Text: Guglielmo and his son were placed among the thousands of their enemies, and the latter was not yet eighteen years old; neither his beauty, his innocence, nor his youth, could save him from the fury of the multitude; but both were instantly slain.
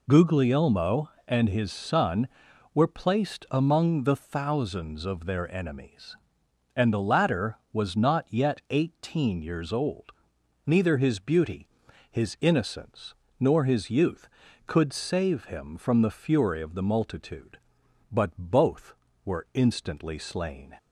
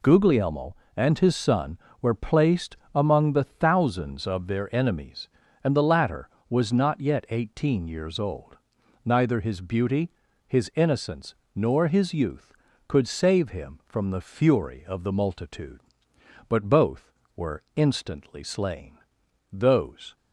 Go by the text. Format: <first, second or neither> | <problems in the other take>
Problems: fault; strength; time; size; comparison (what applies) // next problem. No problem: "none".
first | pauses between "placed" and "among"; slight; at 2.7 s; 0.18 s long // goes on to say "Those"; noticeable; from 19.5 s on; 0.64 s long